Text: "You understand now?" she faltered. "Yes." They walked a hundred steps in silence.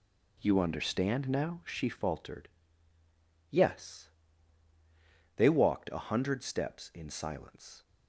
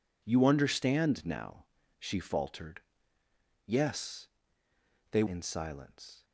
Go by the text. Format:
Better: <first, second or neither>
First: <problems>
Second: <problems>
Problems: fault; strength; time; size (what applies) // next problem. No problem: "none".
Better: first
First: none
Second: skips "walked a hundred steps"; at 5.2 s